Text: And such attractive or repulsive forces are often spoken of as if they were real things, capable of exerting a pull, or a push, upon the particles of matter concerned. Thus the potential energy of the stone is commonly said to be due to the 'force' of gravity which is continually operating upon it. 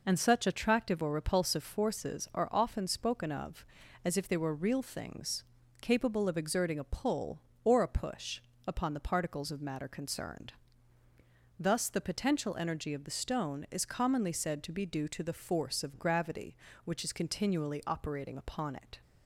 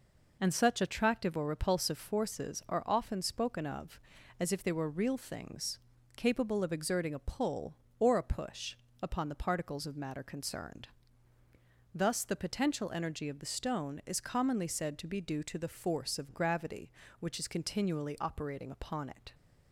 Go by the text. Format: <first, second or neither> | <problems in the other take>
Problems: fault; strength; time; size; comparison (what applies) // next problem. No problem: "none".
neither | none